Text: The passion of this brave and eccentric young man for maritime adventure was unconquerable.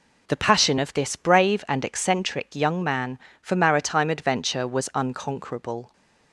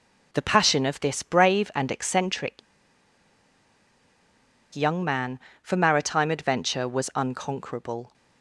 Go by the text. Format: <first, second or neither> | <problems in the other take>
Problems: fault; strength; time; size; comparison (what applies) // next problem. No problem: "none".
first | pauses between "eccentric" and "young"; strong; at 2.5 s; 2.1 s long